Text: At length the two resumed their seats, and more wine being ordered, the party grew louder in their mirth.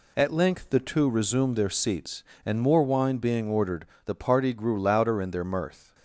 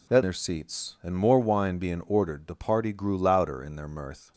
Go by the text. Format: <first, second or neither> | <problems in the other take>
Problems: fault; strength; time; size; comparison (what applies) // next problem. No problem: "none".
first | skips "length the two resumed"; at 0.2 s